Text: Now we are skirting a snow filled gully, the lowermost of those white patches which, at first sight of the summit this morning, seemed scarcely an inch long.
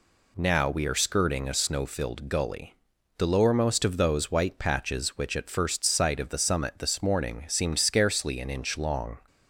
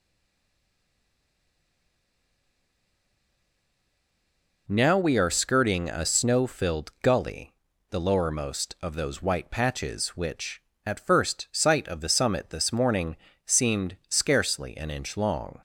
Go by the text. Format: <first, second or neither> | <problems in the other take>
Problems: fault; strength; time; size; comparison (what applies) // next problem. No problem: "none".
first | stays silent before the first word; strong; until 4.6 s; 4.6 s long